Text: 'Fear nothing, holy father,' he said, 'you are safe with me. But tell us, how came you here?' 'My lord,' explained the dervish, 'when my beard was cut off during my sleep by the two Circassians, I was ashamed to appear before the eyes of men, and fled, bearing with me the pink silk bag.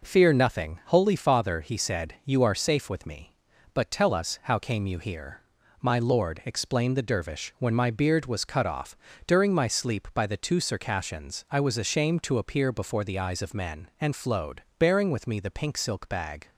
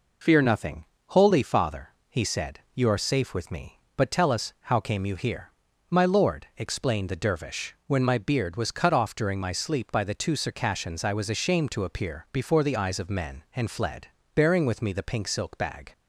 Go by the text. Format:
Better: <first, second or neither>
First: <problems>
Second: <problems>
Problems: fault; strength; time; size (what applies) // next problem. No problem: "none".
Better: second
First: pauses between "off" and "during"; slight; at 8.9 s; 0.28 s long // says "flowed" for "fled"; at 14.1 s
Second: none